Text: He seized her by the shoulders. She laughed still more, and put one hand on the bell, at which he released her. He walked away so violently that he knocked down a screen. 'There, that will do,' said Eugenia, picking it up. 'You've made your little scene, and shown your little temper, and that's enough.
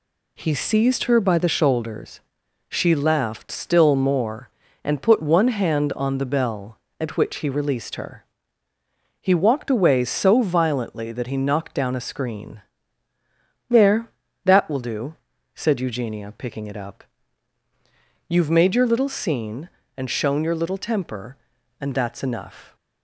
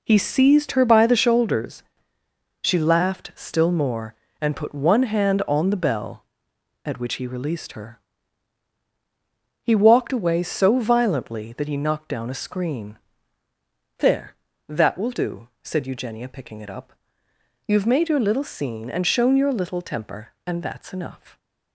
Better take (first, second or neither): neither